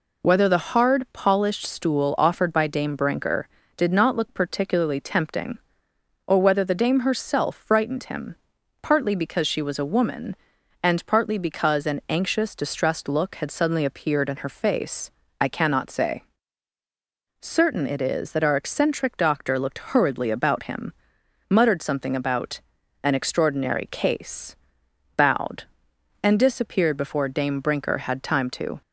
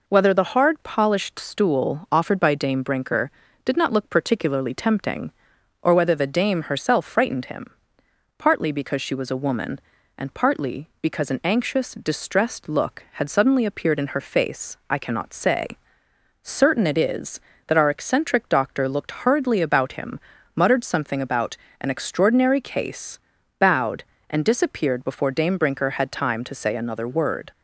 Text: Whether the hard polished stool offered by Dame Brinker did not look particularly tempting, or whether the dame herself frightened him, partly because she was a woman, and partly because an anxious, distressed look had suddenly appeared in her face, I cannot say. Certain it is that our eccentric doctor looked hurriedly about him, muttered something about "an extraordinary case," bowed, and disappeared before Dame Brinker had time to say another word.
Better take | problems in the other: second | pauses between "about" and "an"; at 22.6 s; 0.42 s long; slight in the second // stops before "say another word"; at 28.8 s

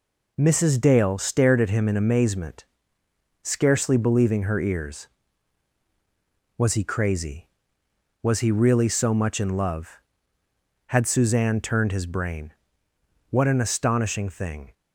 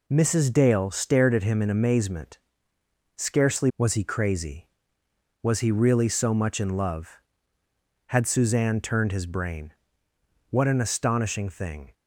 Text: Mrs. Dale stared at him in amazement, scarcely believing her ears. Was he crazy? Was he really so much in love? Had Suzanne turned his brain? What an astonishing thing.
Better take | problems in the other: first | skips "believing her ears"; at 3.7 s

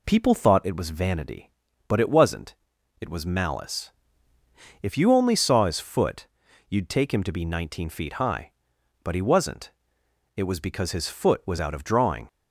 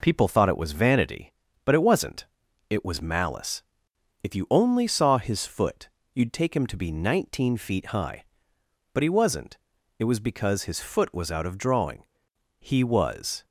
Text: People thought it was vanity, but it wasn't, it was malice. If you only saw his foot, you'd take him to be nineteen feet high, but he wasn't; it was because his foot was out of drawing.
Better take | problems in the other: first | goes on to say "He was"; noticeable; from 12.5 s on; 0.86 s long

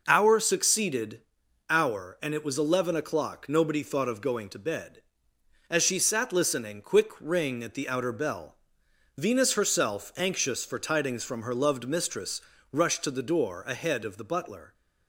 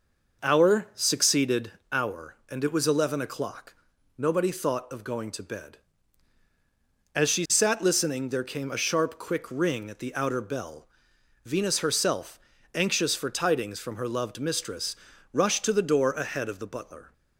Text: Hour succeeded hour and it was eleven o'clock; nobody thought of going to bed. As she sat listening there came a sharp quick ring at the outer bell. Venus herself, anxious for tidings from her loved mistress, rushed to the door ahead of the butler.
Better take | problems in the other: second | pauses between "succeeded" and "hour"; noticeable; at 1.2 s; 0.50 s long; slight in the second // skips "there came a sharp"; at 6.8 s

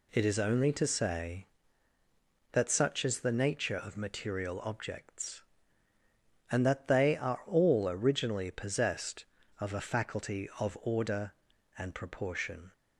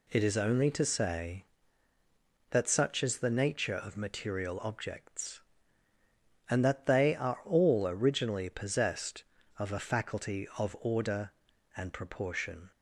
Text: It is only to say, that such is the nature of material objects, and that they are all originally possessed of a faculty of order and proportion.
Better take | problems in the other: neither | none

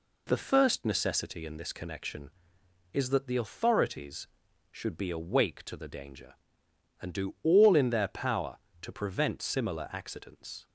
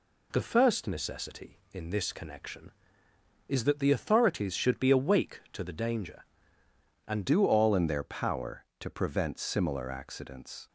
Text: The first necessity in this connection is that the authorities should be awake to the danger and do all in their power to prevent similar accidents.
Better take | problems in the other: first | changes voice at "do"; from 7.2 s on; 3.4 s long

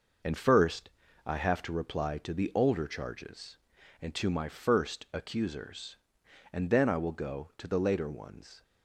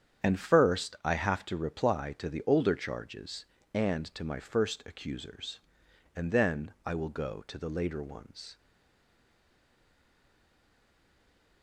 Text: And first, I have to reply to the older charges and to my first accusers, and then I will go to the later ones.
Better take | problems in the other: first | starts louder than the rest; strong; until 1.3 s; 8.5 dB // stays silent after the last word; strong; from 8.5 s on; 3.1 s long

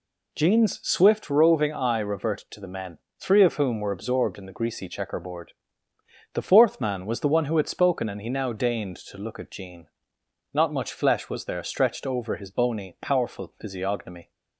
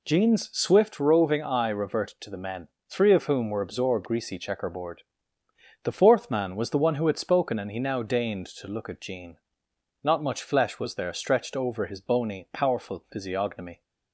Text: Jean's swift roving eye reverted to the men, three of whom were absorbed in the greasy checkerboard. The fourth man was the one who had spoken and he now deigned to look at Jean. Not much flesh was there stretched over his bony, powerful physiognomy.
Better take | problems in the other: first | skips "in the"; at 4.0 s

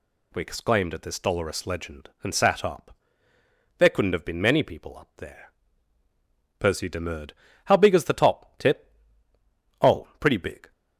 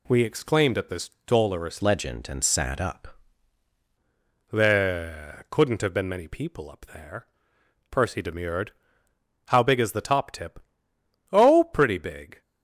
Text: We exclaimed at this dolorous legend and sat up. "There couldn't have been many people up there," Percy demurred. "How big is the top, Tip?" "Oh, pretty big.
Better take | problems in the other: first | pauses between "this" and "dolorous"; slight; at 1.1 s; 0.16 s long // changes voice from "legend" to "up"; from 1.8 to 3.1 s; 1.3 s long

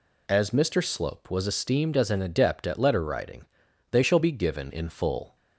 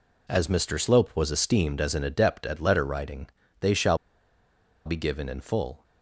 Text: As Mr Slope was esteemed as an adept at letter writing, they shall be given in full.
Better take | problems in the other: first | pauses between "shall" and "be"; noticeable; at 3.9 s; 0.88 s long

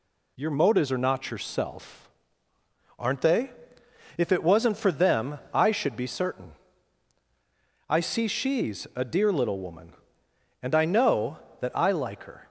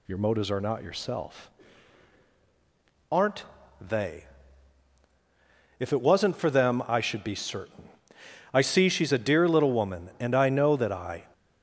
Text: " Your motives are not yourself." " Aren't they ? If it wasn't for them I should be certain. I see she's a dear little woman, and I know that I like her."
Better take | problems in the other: first | pauses between "Aren't" and "they"; slight; at 3.4 s; 0.36 s long // stops before "like her"; at 11.3 s

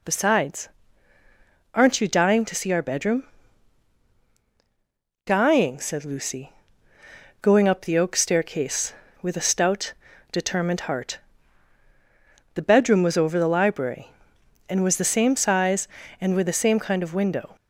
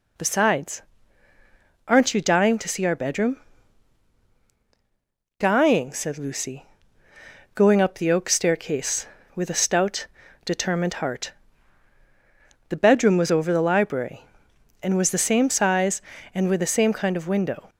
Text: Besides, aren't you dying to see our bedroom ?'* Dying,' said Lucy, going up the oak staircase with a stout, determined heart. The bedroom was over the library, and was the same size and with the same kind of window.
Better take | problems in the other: neither | none

